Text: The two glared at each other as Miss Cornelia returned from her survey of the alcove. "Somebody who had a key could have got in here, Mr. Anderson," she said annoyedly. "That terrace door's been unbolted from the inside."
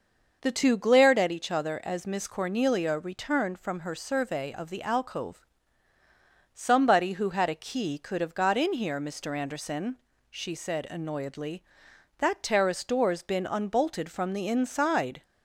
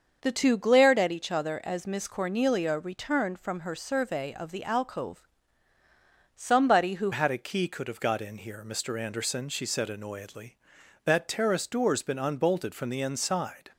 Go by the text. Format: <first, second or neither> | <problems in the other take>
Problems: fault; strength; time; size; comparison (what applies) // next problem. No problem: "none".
first | starts louder than the rest; until 1.2 s; 6.5 dB; noticeable in the first // changes voice at "had"; from 7.1 s on; 6.5 s long